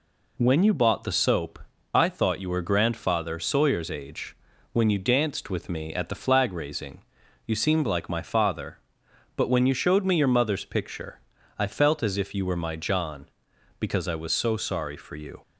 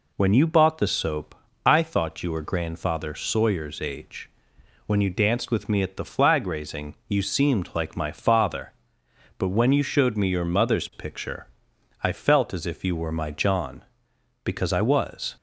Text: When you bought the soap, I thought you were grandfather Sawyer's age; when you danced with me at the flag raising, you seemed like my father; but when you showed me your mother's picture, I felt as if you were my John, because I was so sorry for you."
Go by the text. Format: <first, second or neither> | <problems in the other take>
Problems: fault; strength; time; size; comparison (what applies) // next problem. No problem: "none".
first | stops before "so sorry for you"; at 15.3 s